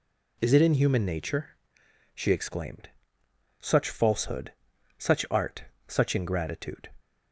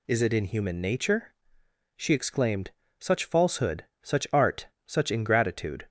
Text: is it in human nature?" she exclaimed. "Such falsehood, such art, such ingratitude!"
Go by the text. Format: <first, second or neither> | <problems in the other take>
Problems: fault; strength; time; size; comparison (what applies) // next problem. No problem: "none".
neither | none